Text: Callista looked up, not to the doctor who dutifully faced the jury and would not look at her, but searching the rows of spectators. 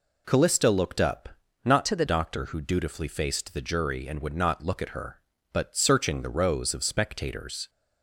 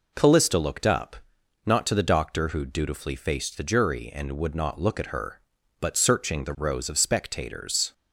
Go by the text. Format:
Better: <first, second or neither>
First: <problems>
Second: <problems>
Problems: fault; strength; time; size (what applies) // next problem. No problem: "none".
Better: second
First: changes voice from "to" to "the"; from 1.8 to 2.0 s; 0.2 s long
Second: none